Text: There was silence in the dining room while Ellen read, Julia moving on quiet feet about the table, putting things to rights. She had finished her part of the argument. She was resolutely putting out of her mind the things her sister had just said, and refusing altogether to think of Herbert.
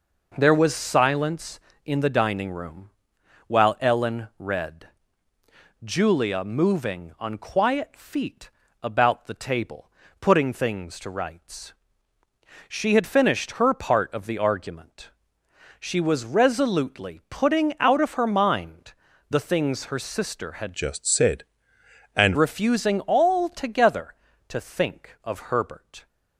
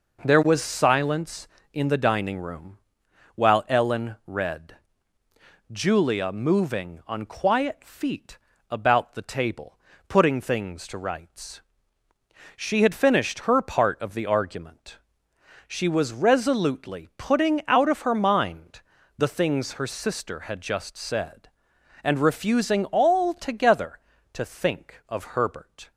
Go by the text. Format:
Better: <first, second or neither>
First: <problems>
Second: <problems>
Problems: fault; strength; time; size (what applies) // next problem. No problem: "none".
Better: second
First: pauses between "room" and "while"; noticeable; at 2.8 s; 0.58 s long // pauses between "feet" and "about"; slight; at 8.4 s; 0.32 s long // pauses between "mind" and "the"; slight; at 18.9 s; 0.36 s long // changes voice from "just" to "and"; from 20.7 to 22.3 s; 1.6 s long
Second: pauses between "room" and "while"; noticeable; at 2.7 s; 0.58 s long // pauses between "feet" and "about"; slight; at 8.3 s; 0.32 s long // pauses between "mind" and "the"; slight; at 18.8 s; 0.36 s long